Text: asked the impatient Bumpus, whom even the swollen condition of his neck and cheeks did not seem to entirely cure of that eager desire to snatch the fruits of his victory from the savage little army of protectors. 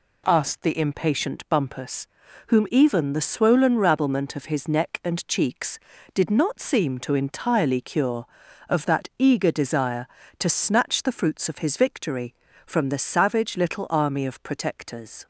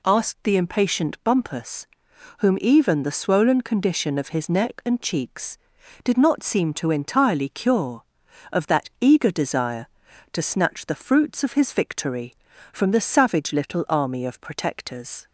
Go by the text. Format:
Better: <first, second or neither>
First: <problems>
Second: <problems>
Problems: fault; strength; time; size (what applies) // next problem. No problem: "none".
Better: second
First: says "rabblement" for "condition"; at 3.7 s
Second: none